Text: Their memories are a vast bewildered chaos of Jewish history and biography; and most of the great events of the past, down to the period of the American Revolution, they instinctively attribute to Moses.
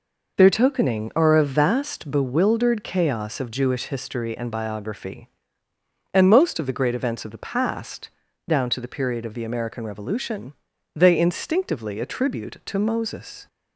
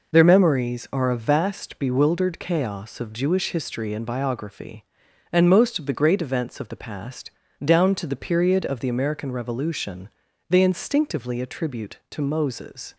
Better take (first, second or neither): second